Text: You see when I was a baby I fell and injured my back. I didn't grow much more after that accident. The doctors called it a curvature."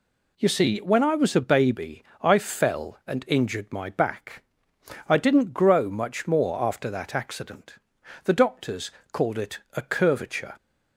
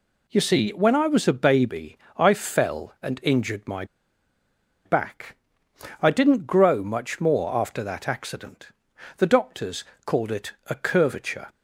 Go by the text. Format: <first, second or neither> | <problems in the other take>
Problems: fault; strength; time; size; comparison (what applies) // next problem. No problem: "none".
first | pauses between "baby" and "I"; slight; at 1.9 s; 0.20 s long; slight in the first // pauses between "my" and "back"; at 3.8 s; 1.0 s long // pauses between "doctors" and "called"; slight; at 9.8 s; 0.22 s long; slight in the first